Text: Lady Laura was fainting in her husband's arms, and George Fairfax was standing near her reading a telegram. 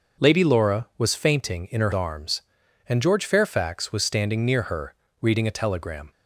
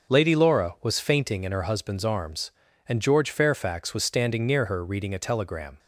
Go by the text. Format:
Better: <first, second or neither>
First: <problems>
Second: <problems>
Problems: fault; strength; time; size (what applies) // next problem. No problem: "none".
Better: second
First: starts louder than the rest; until 1.2 s; 6 dB // skips "husband's"; at 1.9 s // pauses between "her" and "reading"; slight; at 4.9 s; 0.26 s long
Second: starts louder than the rest; until 1.1 s; 7 dB